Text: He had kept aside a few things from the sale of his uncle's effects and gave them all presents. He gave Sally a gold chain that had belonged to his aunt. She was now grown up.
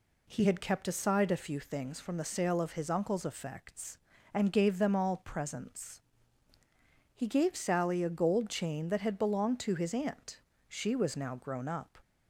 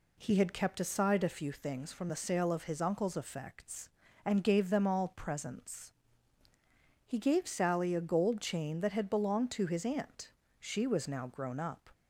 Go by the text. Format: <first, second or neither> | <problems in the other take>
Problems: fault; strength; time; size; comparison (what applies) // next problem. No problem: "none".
neither | none